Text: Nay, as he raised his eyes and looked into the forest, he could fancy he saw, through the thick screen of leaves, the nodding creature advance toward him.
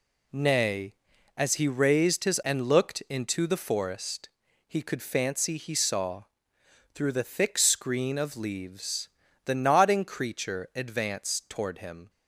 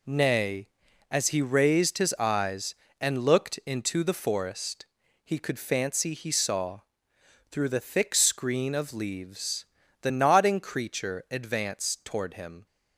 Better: second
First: skips "eyes"; at 2.4 s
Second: none

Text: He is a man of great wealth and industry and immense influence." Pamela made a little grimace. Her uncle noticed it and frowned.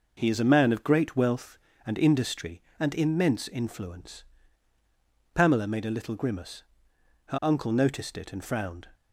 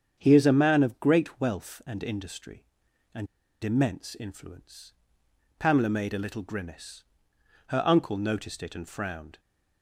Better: first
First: none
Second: starts louder than the rest; strong; until 1.1 s; 7.5 dB // pauses between "and" and "immense"; at 3.2 s; 0.36 s long

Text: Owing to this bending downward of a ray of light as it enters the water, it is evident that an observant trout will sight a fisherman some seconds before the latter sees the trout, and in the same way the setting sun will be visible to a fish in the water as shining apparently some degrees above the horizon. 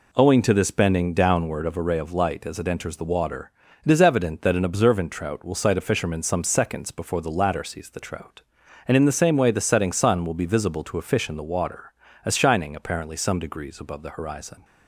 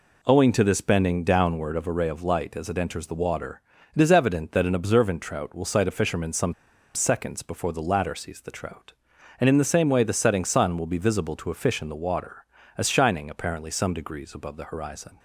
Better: first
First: none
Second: pauses between "some" and "seconds"; at 6.5 s; 0.41 s long

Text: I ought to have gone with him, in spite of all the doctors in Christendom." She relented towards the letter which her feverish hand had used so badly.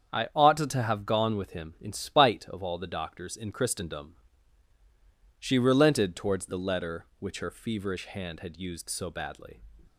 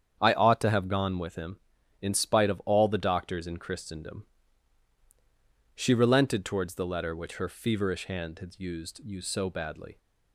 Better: first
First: starts louder than the rest; strong; until 1.1 s; 8 dB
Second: starts louder than the rest; strong; until 1.2 s; 8 dB // says "used" twice; at 9.0 s

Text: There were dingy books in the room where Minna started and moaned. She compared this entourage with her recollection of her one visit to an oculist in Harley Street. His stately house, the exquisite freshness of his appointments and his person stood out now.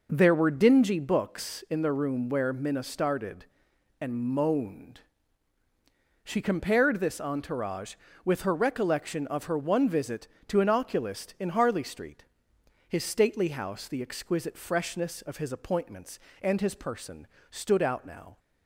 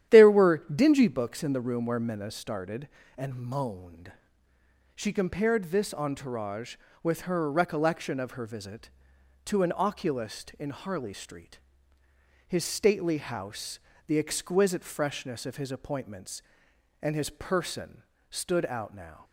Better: first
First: pauses between "person" and "stood"; slight; at 17.2 s; 0.24 s long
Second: starts louder than the rest; strong; until 1.2 s; 11 dB // skips "one"; at 8.4 s // pauses between "person" and "stood"; slight; at 18.0 s; 0.26 s long

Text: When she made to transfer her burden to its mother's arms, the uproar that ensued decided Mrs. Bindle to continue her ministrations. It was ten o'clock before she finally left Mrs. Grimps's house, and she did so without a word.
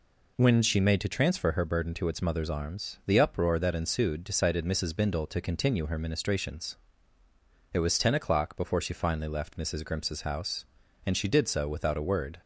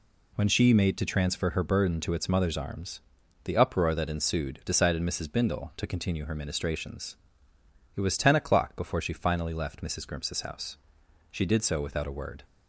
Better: first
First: none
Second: skips "and"; at 11.0 s

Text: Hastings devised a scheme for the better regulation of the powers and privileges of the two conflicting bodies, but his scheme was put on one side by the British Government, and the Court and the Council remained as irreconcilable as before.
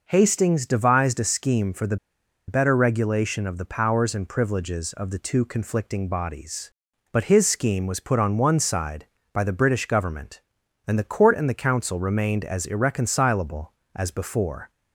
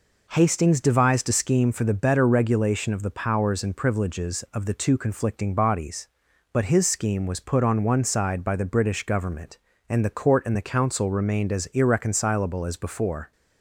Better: second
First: pauses between "the" and "better"; noticeable; at 1.9 s; 0.51 s long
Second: none

